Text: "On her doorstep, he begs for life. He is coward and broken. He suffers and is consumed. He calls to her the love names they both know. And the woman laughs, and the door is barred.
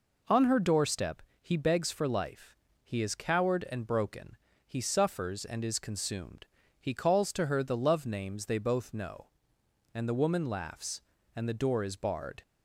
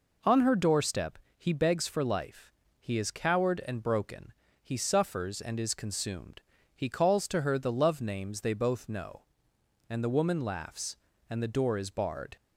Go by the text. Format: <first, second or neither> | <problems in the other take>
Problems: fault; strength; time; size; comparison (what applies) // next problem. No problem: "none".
neither | none